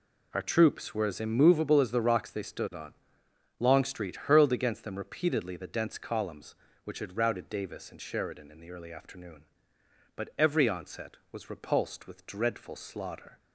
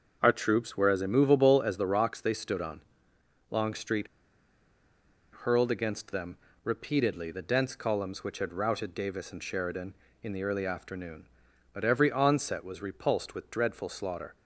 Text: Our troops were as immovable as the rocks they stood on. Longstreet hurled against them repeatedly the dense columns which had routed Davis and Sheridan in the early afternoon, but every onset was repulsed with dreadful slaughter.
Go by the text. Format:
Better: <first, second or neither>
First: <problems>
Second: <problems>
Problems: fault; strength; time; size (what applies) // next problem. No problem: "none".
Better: first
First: none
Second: starts louder than the rest; until 1.2 s; 6.5 dB // pauses between "Longstreet" and "hurled"; strong; at 4.0 s; 1.3 s long // pauses between "them" and "repeatedly"; slight; at 6.3 s; 0.26 s long